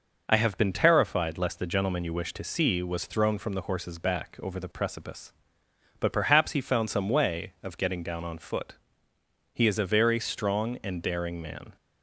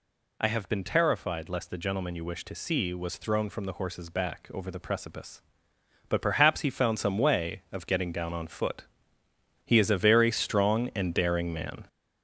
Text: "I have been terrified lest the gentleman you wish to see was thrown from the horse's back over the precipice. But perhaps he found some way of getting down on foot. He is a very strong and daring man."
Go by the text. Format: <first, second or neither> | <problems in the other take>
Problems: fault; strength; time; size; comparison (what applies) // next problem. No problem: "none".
first | gets louder; noticeable; throughout; 5.5 dB